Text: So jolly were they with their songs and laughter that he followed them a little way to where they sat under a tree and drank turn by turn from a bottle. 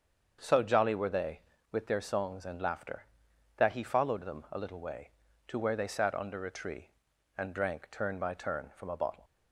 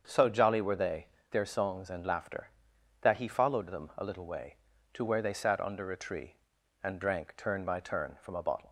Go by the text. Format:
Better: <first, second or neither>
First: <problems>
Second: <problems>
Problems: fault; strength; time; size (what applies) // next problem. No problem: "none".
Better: first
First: starts louder than the rest; until 1.4 s; 7 dB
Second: starts louder than the rest; until 1.0 s; 7 dB // skips "with"; at 1.1 s